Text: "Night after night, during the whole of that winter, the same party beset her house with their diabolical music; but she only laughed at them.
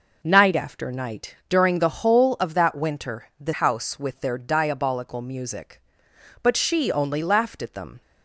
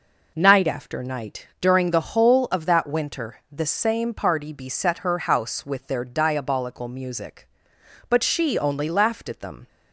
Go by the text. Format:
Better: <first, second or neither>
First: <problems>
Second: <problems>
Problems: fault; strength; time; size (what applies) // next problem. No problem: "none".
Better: second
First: skips "same party beset her"; at 3.5 s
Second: none